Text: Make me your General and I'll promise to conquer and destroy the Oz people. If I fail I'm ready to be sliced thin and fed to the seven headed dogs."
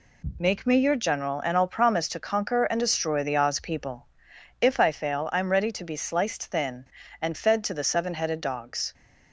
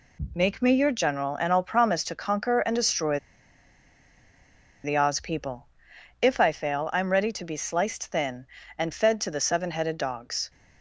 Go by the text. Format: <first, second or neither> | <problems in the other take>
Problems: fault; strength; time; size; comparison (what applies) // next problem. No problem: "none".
first | pauses between "destroy" and "the"; strong; at 3.1 s; 1.6 s long